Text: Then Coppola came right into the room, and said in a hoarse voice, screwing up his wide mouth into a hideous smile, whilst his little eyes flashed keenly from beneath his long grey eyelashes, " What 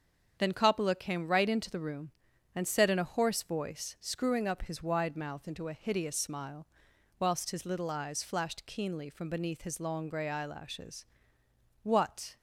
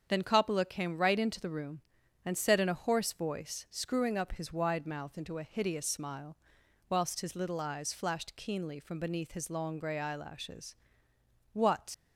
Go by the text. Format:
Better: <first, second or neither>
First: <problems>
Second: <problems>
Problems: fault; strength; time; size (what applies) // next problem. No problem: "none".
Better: first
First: starts louder than the rest; strong; until 1.4 s; 7.5 dB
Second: starts louder than the rest; strong; until 1.1 s; 7.5 dB // leaves "What" unfinished; at 11.9 s; 125 ms